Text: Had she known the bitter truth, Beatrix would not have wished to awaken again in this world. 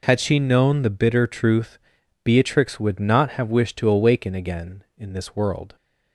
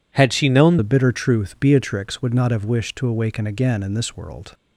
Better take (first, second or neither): first